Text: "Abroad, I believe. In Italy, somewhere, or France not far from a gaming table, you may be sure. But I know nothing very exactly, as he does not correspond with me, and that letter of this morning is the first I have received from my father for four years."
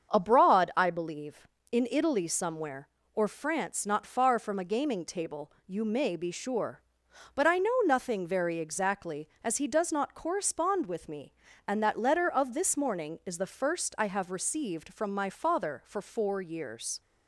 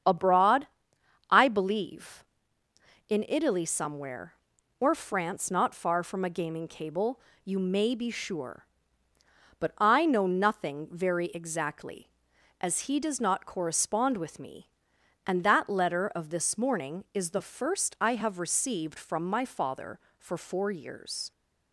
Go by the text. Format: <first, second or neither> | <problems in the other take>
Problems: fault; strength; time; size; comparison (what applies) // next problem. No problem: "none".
first | starts louder than the rest; strong; until 1.6 s; 8 dB; strong in the first // says "cable" for "table"; at 6.6 s